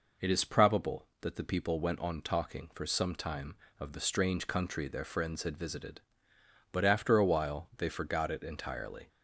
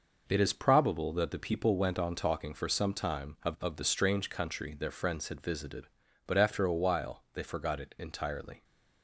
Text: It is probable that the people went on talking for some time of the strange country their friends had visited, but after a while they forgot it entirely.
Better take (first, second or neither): first